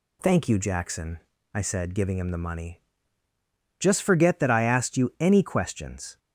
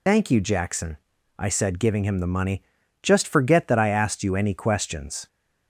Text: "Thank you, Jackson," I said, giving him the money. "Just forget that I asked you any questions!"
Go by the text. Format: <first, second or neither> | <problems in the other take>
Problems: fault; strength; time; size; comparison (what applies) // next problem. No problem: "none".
first | loses the start of "Thank"; at 0.0 s; 70 ms